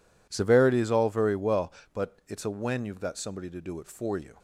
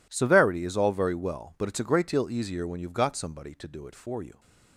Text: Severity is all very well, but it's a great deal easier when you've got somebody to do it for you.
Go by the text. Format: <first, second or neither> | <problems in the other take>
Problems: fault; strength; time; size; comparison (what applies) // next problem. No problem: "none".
second | skips "great deal easier"; at 2.4 s